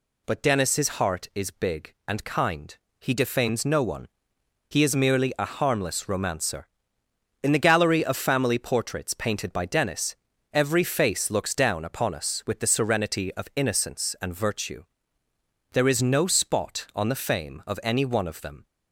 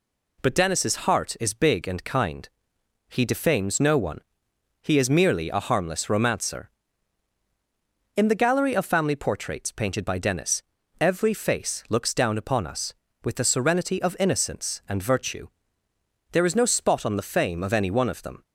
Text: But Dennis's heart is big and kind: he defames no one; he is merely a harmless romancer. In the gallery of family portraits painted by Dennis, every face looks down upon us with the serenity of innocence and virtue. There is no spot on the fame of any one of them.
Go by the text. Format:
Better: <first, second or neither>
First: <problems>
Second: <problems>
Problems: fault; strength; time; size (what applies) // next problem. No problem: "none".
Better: neither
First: none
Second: none